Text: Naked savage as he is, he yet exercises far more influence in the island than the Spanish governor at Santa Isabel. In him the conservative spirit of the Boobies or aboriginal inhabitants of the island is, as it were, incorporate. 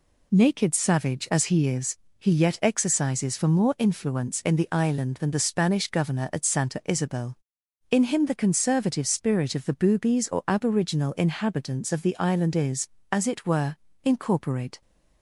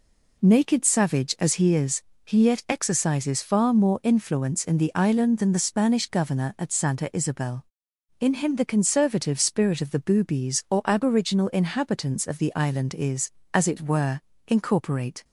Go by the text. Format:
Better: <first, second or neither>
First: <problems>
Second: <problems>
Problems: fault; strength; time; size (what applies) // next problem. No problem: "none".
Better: second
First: says "for" for "far"; at 3.3 s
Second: none